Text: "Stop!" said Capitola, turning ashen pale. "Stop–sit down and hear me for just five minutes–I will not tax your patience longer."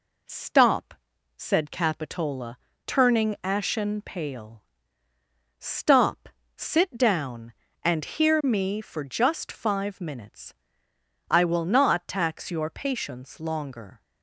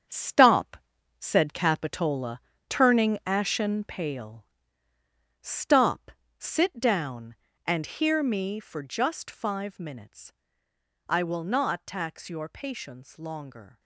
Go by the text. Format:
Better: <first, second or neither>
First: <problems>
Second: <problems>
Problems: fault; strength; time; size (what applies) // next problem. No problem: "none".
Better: first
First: none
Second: gets quieter; strong; throughout; 8 dB